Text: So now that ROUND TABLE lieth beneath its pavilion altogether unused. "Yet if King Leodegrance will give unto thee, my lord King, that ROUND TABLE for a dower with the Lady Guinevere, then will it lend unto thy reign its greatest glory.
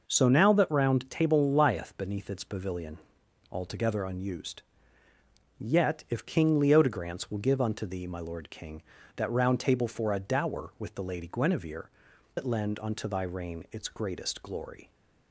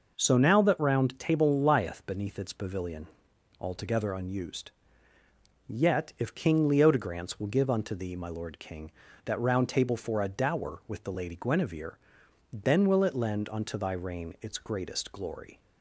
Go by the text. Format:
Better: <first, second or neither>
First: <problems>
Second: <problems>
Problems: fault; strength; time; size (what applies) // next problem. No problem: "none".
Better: second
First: pauses between "pavilion" and "altogether"; noticeable; at 2.9 s; 0.52 s long // skips "then will"; at 12.1 s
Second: pauses between "pavilion" and "altogether"; noticeable; at 3.0 s; 0.52 s long